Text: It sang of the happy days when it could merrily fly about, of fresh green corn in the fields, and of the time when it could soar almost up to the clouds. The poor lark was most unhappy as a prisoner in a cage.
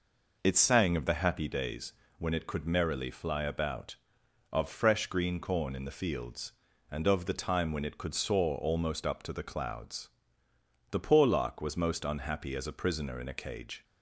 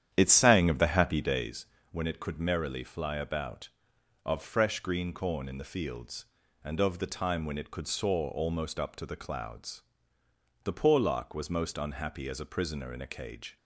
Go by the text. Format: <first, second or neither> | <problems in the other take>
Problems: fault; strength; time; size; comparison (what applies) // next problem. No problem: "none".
first | starts louder than the rest; strong; until 1.6 s; 10 dB // pauses between "days" and "when"; slight; at 1.6 s; 0.26 s long; slight in the first